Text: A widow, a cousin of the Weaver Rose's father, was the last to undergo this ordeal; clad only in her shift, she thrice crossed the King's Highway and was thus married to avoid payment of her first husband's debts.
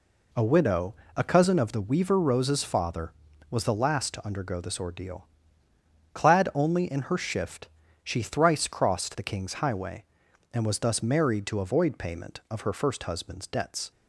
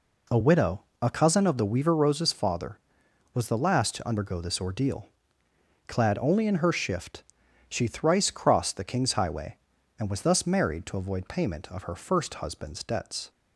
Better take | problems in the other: neither | none

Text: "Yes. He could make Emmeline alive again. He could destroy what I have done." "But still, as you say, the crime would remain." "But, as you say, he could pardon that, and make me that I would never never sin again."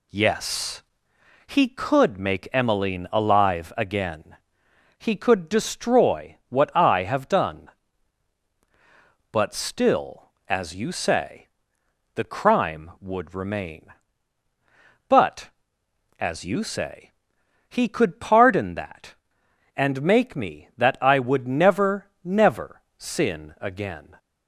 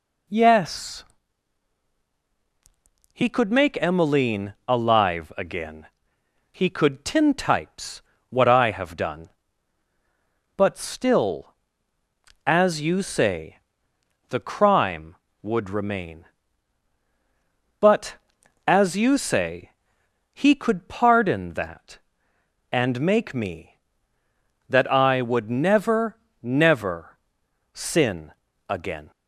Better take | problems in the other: first | pauses between "Emmeline" and "alive"; slight; at 4.5 s; 0.16 s long // says "tintypes" for "destroy"; at 7.0 s // pauses between "never" and "never"; slight; at 26.1 s; 0.26 s long; slight in the first // pauses between "never" and "sin"; noticeable; at 27.1 s; 0.56 s long; slight in the first // pauses between "sin" and "again"; slight; at 28.3 s; 0.34 s long

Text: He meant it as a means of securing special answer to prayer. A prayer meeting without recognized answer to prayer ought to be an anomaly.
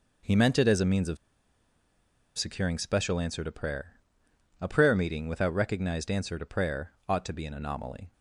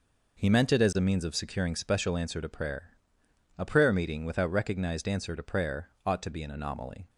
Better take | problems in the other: second | pauses between "of" and "securing"; at 1.1 s; 1.2 s long // pauses between "prayer" and "ought"; slight; at 6.9 s; 0.16 s long; slight in the second

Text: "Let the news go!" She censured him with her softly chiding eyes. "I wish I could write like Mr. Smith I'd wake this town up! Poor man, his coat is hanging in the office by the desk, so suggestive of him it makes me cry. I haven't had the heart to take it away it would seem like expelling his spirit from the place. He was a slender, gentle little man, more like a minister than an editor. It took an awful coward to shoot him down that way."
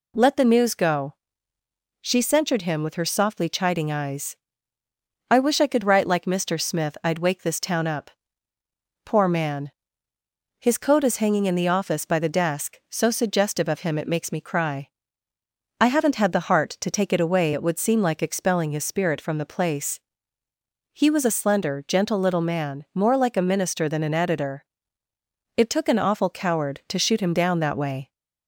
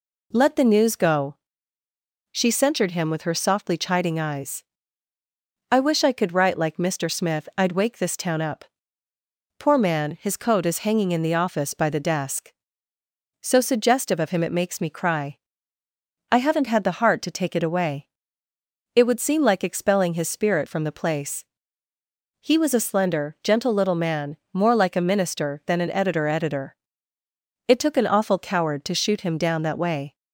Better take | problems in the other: first | pauses between "away" and "it"; noticeable; at 18.0 s; 0.90 s long // says "editor" twice; at 26.2 s

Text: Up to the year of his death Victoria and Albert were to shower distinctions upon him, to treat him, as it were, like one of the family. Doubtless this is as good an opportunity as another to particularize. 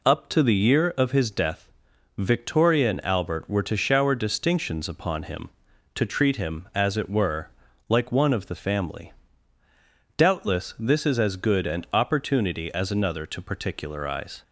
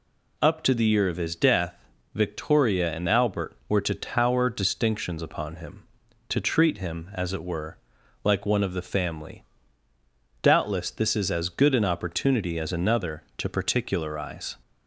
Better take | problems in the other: first | pauses between "death" and "Victoria"; at 1.7 s; 0.40 s long; noticeable in the first // says "tower" for "shower"; at 3.9 s

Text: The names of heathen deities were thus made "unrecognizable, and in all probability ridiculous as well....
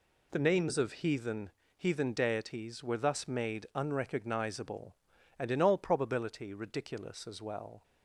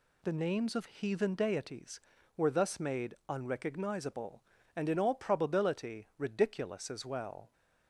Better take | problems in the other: second | says "heathen" twice; at 1.7 s

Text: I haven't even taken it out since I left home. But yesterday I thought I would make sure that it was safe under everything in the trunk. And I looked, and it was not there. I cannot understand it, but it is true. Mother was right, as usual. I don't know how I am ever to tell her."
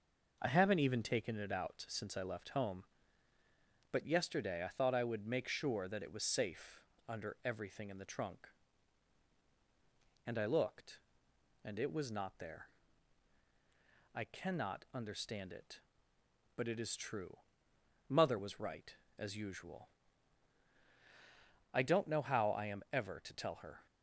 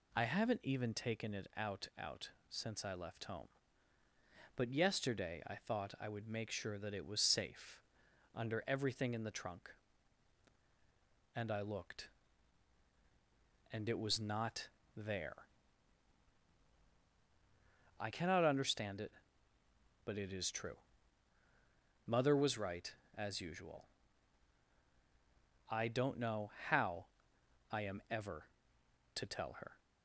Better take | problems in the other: first | says "out" twice; at 1.9 s // pauses between "safe" and "under"; noticeable; at 7.8 s; 0.54 s long; slight in the first // pauses between "not" and "there"; slight; at 14.6 s; 0.26 s long // pauses between "know" and "how"; slight; at 26.5 s; 0.18 s long // pauses between "how" and "I"; noticeable; at 27.0 s; 0.66 s long

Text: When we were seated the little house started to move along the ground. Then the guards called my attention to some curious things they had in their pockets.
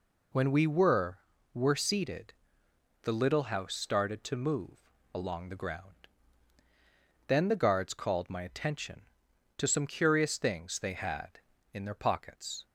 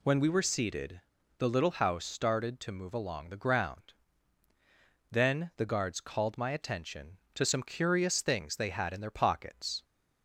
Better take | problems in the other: second | says "were" twice; at 1.5 s // pauses between "seated" and "the"; noticeable; at 2.3 s; 0.70 s long; slight in the second // pauses between "move" and "along"; slight; at 4.9 s; 0.23 s long

